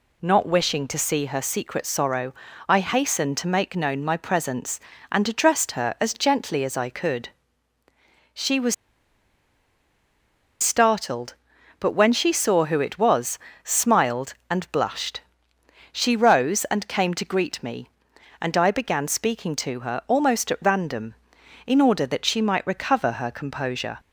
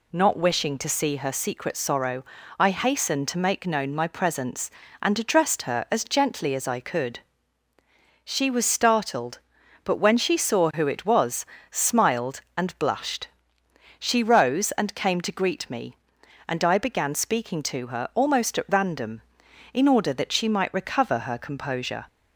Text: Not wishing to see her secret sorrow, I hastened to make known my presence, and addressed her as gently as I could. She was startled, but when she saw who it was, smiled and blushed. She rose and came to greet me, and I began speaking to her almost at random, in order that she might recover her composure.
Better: second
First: pauses between "was" and "startled"; strong; at 8.7 s; 1.8 s long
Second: none

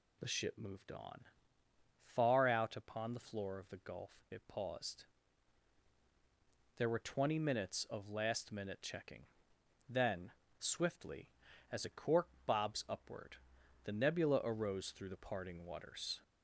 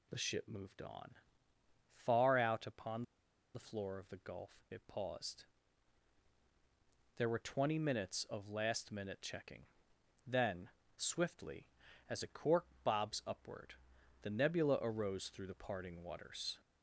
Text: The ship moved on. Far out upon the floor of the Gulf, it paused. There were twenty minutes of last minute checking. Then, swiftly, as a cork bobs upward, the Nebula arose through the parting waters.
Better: first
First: pauses between "cork" and "bobs"; slight; at 12.2 s; 0.20 s long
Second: pauses between "upon" and "the"; noticeable; at 3.0 s; 0.51 s long // pauses between "cork" and "bobs"; slight; at 12.6 s; 0.20 s long

